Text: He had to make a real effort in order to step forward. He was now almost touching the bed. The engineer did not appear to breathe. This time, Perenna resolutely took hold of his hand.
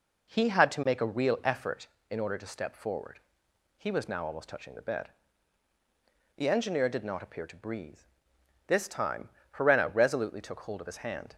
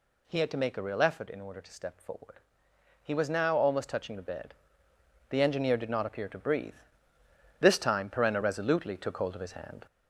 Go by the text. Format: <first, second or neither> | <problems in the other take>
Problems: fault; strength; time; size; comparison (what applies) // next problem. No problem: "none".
first | gets louder; noticeable; throughout; 4.5 dB